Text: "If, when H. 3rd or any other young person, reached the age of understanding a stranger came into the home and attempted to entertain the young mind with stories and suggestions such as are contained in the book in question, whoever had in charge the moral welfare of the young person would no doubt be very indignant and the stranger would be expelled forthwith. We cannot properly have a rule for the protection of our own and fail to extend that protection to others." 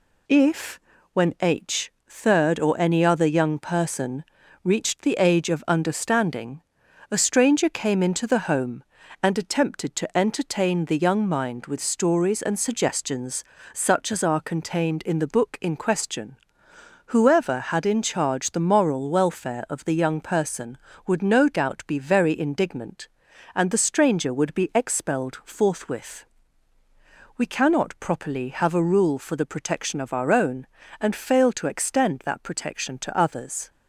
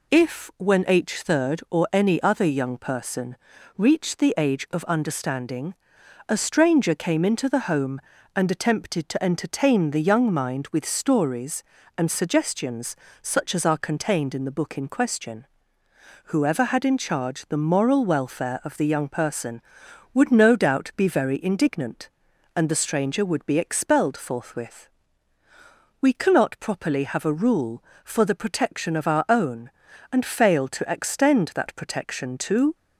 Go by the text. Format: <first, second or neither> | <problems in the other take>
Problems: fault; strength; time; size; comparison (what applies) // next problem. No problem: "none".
first | pauses between "understanding" and "a"; noticeable; at 5.7 s; 0.54 s long; noticeable in the first // pauses between "suggestions" and "such"; slight; at 12.9 s; 0.24 s long; slight in the first // stops before "others"; at 32.7 s